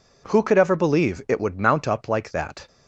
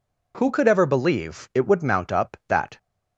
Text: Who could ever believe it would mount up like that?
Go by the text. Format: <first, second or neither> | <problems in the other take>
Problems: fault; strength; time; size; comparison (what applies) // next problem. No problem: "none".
first | skips "like"; at 2.4 s